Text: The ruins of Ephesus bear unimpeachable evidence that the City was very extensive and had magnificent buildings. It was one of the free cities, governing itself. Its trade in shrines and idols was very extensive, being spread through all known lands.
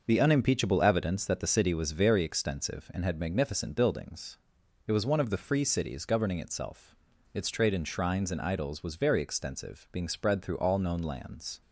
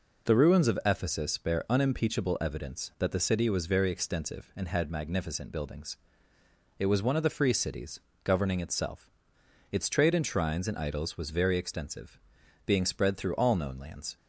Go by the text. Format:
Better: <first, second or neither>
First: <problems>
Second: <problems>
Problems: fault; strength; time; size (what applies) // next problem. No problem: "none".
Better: second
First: starts louder than the rest; noticeable; until 1.0 s; 6 dB // skips "ruins of Ephesus bear"; at 0.1 s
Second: none